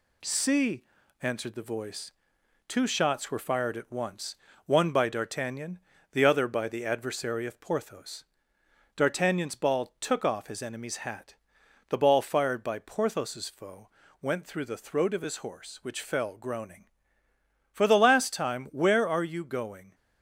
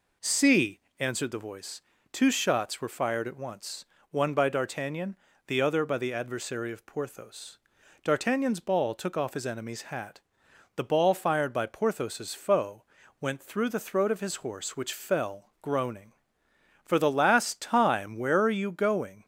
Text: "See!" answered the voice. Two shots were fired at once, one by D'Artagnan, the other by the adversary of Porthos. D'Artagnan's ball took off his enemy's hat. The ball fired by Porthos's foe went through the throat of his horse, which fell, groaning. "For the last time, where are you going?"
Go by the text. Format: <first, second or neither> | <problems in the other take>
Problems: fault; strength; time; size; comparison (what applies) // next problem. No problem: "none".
second | gets quieter; slight; throughout; 2.5 dB // pauses between "foe" and "went"; slight; at 13.8 s; 0.32 s long; also in the second